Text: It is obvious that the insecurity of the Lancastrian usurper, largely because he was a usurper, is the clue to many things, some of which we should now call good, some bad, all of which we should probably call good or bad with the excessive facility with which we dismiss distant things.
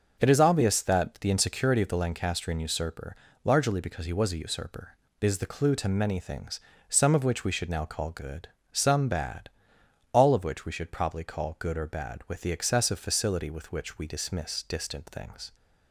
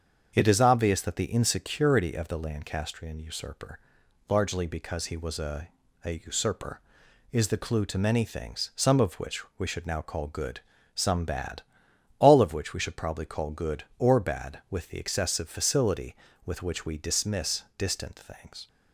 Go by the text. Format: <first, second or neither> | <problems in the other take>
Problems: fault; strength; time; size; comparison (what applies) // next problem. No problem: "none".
first | starts louder than the rest; until 1.3 s; 7 dB; also in the first // says "a" twice; at 6.0 s